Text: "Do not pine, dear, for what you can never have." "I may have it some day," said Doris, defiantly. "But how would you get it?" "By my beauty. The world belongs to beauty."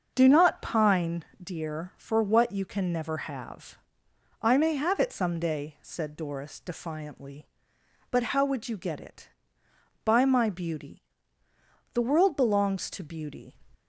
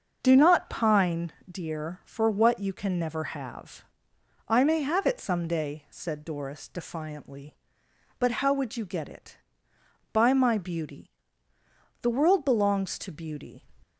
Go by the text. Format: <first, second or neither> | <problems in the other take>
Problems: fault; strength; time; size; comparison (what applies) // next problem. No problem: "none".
neither | starts louder than the rest; the same in both